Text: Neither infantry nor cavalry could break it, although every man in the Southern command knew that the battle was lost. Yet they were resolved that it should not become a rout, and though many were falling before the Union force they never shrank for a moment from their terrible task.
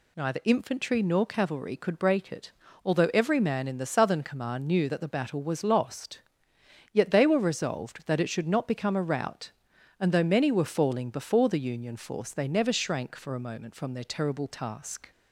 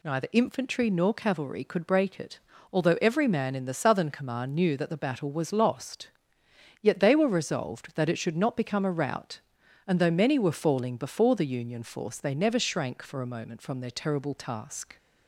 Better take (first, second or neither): neither